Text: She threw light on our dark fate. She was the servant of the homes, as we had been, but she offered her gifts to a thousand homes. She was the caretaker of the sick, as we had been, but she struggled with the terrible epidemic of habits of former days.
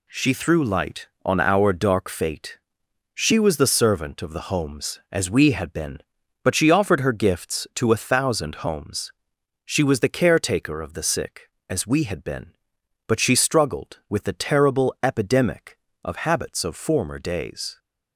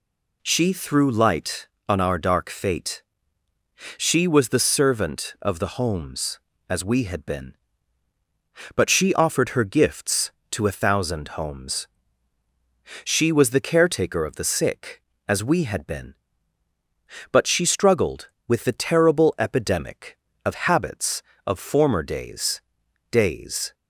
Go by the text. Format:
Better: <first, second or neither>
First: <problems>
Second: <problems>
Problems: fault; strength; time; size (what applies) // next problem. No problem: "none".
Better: first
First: none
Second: says "days" twice; at 23.1 s